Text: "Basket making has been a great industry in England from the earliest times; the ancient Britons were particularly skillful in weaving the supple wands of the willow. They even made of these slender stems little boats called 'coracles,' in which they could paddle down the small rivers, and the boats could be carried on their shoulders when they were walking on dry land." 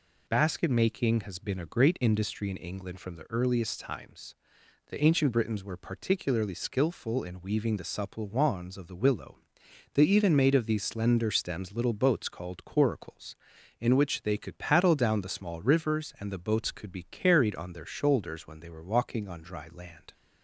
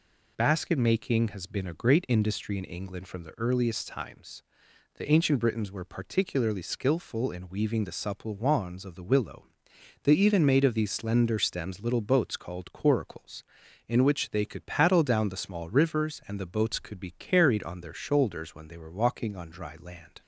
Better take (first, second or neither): neither